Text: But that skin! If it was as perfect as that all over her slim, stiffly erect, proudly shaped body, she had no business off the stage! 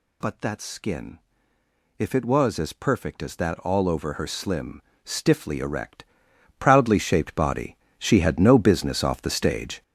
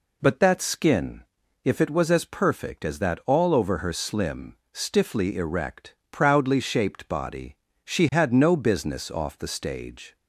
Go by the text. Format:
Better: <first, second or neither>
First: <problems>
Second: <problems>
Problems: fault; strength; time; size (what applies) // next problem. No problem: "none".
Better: second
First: gets louder; strong; throughout; 8.5 dB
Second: none